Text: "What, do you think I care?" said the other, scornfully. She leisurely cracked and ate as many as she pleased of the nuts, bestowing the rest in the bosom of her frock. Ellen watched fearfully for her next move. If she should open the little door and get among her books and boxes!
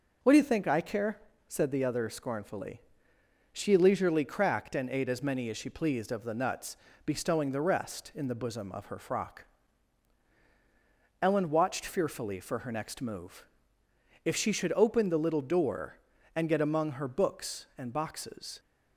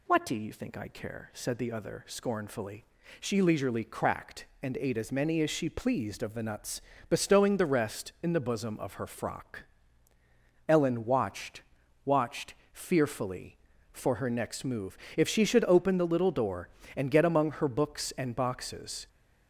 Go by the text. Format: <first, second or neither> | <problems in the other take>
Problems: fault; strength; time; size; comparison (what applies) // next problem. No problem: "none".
first | says "watched" twice; at 12.0 s